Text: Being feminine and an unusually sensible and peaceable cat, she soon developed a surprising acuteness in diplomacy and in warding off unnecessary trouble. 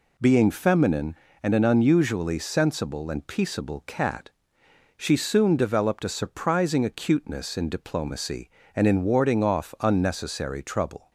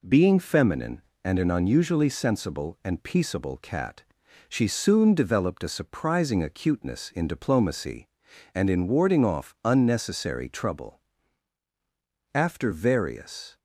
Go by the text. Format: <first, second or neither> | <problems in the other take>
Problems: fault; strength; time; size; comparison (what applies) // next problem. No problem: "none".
first | goes on to say "After various"; noticeable; from 12.3 s on; 1.2 s long